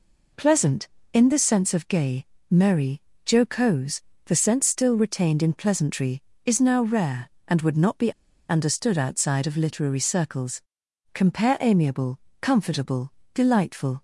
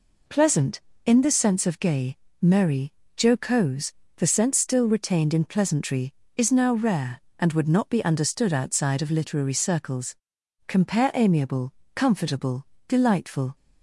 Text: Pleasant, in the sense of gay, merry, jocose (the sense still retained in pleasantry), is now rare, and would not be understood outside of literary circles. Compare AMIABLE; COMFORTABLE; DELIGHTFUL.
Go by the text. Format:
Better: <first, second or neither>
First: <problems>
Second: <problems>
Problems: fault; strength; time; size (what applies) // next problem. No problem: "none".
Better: second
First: pauses between "be" and "understood"; at 8.1 s; 0.37 s long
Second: none